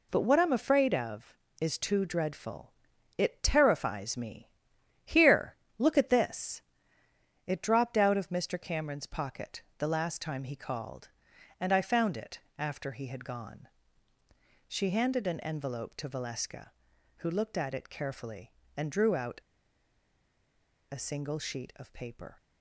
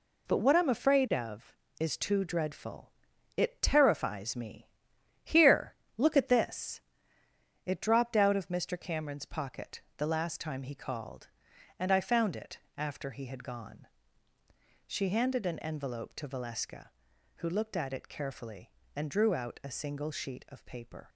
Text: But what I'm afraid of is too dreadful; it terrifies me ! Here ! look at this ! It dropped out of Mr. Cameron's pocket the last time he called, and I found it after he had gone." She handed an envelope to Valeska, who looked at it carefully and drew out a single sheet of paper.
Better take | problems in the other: second | pauses between "pocket" and "the"; slight; at 9.6 s; 0.16 s long; slight in the second // pauses between "it" and "after"; slight; at 12.3 s; 0.18 s long; slight in the second // pauses between "out" and "a"; strong; at 19.3 s; 1.5 s long

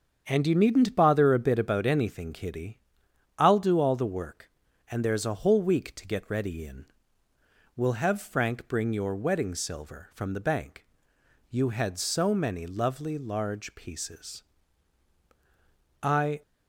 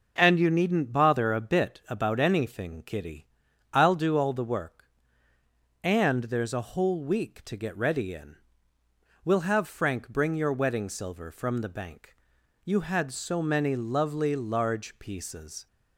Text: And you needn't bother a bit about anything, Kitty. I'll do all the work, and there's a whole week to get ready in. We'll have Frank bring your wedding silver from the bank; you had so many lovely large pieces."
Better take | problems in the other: second | starts louder than the rest; strong; until 1.2 s; 7.5 dB // goes on to say "I"; slight; from 16.0 s on; 0.38 s long

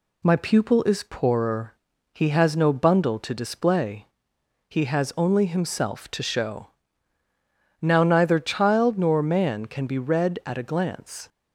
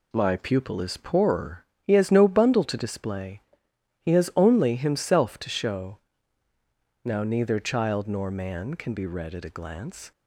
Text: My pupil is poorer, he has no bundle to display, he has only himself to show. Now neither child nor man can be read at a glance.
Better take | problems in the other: first | gets quieter; noticeable; throughout; 5.5 dB

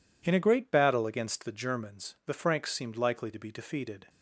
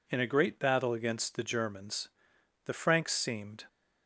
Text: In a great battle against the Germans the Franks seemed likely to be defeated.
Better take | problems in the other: first | pauses between "Germans" and "the"; noticeable; at 2.0 s; 0.56 s long // stops before "likely to be defeated"; at 3.6 s

